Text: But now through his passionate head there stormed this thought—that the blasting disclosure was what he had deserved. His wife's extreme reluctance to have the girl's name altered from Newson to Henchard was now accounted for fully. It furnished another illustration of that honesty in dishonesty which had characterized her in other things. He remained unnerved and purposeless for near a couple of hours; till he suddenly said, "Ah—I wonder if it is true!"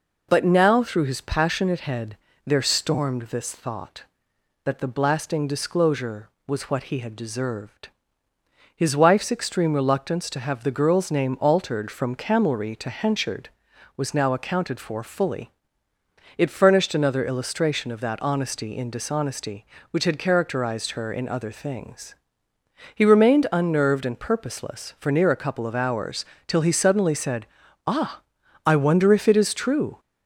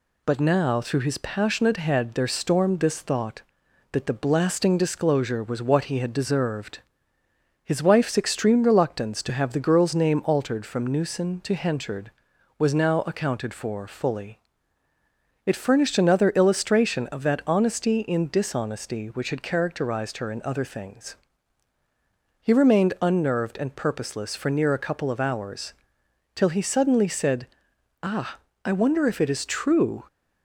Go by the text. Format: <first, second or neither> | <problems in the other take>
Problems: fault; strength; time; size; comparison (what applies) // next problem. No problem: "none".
second | pauses between "head" and "there"; slight; at 2.1 s; 0.30 s long // says "Camelry" for "Newson"; at 12.1 s